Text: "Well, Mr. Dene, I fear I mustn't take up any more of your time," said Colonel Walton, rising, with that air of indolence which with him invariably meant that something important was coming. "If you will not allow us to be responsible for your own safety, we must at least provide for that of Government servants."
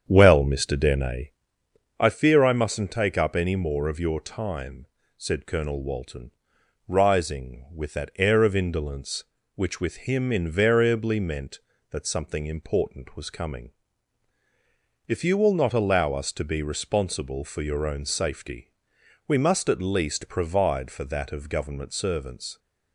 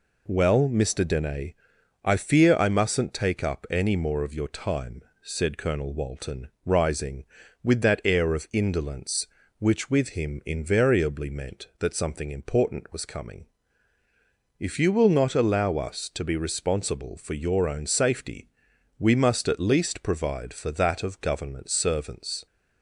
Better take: second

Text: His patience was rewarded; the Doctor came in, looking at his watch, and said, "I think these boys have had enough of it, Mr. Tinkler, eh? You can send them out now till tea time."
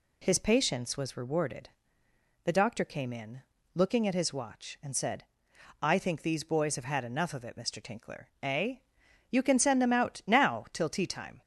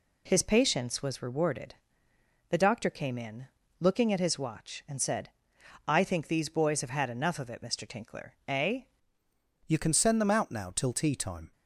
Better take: first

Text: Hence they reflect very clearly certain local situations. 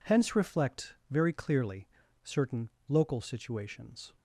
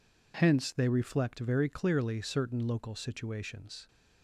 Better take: second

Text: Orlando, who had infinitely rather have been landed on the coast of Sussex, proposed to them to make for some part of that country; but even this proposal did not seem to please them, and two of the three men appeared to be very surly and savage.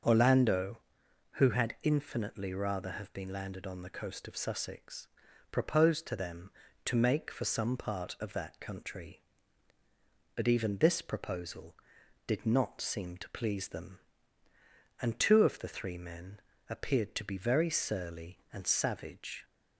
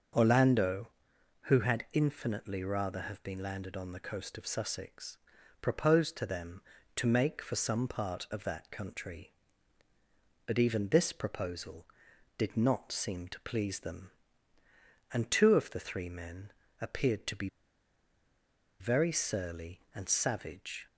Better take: first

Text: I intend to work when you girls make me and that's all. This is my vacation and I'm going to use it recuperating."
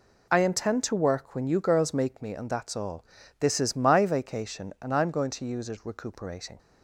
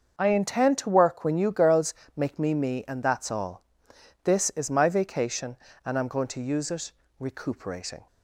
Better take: first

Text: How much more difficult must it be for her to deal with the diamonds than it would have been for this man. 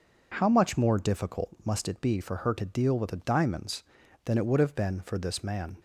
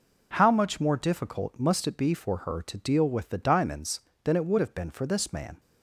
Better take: neither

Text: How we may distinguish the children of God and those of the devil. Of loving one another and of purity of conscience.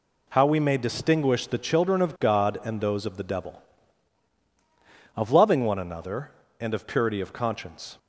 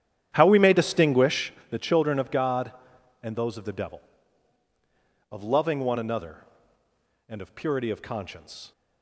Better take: first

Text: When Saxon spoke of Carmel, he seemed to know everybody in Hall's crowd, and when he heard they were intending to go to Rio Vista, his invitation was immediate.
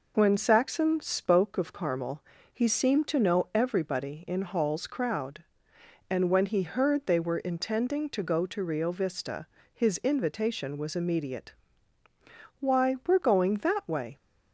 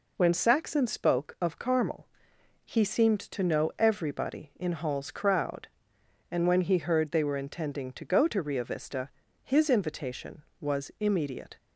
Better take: second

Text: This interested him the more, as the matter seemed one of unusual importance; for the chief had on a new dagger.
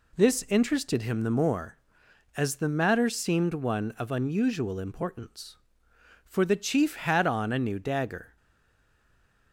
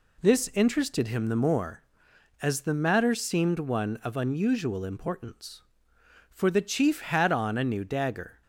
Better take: second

